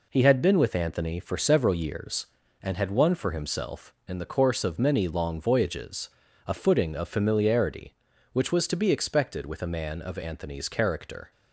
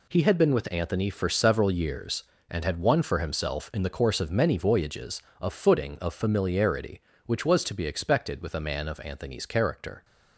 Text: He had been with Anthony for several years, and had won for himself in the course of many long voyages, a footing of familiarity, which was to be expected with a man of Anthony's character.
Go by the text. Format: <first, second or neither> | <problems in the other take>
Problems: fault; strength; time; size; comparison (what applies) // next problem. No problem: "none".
first | skips "long"; at 4.5 s